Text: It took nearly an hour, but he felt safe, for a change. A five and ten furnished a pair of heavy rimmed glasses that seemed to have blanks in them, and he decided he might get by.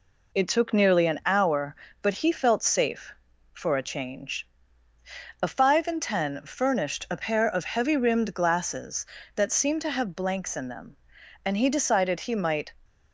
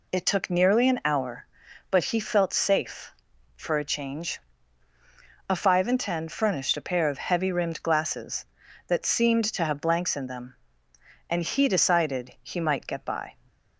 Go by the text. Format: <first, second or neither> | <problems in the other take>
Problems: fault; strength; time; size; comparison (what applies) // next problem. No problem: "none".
second | stops before "get by"; at 12.8 s